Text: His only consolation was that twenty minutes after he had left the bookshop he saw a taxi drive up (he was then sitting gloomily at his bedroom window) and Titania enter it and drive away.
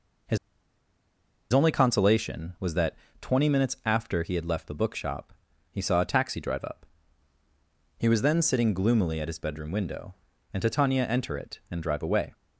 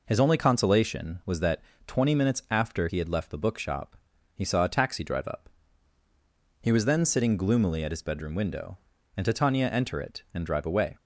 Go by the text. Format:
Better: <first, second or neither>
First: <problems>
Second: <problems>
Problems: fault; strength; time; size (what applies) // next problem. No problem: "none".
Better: second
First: pauses between "His" and "only"; at 0.3 s; 1.1 s long // pauses between "that" and "twenty"; slight; at 2.9 s; 0.26 s long // pauses between "bookshop" and "he"; at 5.3 s; 0.38 s long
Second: pauses between "that" and "twenty"; slight; at 1.6 s; 0.26 s long // pauses between "bookshop" and "he"; at 3.9 s; 0.38 s long